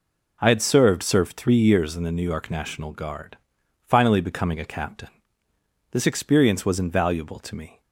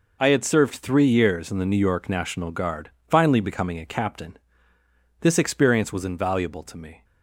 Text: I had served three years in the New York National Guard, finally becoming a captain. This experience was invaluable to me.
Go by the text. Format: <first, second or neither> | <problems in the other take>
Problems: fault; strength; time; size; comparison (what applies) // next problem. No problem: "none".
second | says "served" twice; at 1.0 s